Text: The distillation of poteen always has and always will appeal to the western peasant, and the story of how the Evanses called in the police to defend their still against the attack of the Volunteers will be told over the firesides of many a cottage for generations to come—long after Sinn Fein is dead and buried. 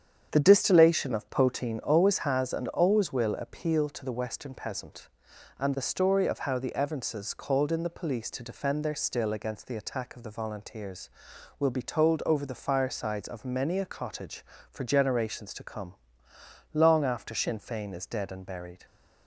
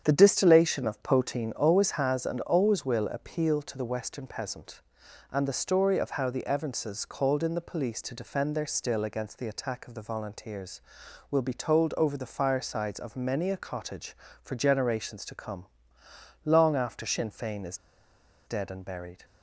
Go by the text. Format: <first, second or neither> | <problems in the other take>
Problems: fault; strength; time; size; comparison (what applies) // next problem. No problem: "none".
first | starts louder than the rest; strong; until 1.0 s; 8.5 dB; strong in the first // pauses between "is" and "dead"; noticeable; at 17.7 s; 0.68 s long